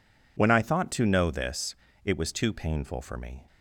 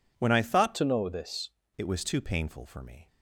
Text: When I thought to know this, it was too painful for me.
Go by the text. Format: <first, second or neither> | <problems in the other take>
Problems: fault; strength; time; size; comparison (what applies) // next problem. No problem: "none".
first | changes voice from "to" to "this"; from 0.7 to 1.5 s; 0.8 s long